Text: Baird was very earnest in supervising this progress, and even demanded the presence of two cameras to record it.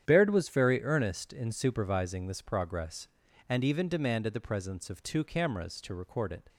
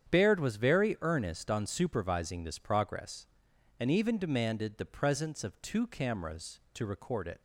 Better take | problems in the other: first | starts louder than the rest; strong; until 1.1 s; 8.5 dB; strong in the first // says "on" for "in"; at 1.5 s

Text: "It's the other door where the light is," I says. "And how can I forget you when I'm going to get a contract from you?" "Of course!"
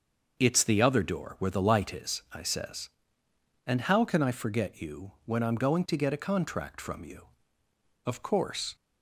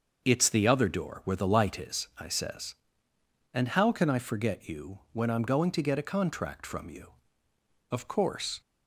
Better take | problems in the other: neither | starts louder than the rest; the same in both

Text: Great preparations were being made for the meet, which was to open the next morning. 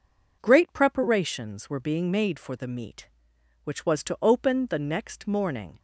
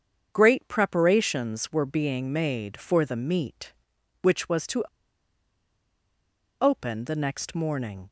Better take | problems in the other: first | starts louder than the rest; strong; until 1.3 s; 7.5 dB // pauses between "to" and "open"; strong; at 4.8 s; 1.7 s long

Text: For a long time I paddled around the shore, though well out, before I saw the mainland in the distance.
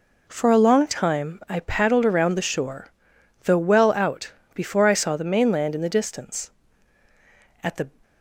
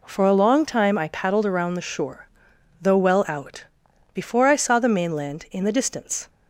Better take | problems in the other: second | goes on to say "At the"; slight; from 7.6 s on; 0.26 s long

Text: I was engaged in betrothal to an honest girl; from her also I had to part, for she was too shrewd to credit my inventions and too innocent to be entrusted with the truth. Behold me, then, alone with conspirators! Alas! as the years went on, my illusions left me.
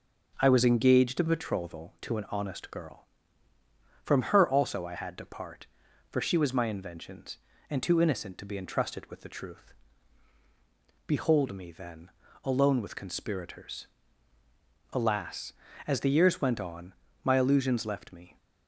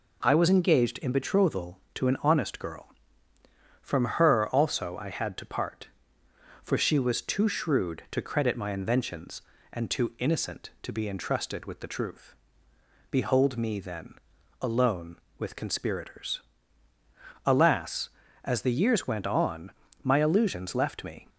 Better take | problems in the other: second | skips "too shrewd to credit"; at 6.5 s

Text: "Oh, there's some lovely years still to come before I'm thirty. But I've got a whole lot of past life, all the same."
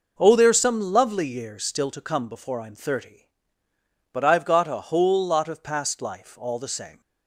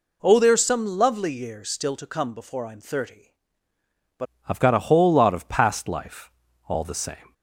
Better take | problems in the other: first | changes voice at "I've"; from 4.4 s on; 2.9 s long

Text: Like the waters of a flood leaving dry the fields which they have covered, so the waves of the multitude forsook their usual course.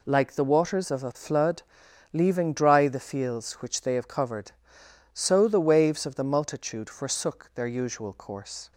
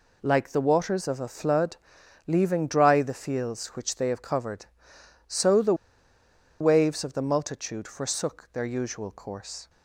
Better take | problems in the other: first | pauses between "flood" and "leaving"; noticeable; at 1.7 s; 0.50 s long; noticeable in the first // pauses between "the" and "waves"; noticeable; at 5.7 s; 0.86 s long

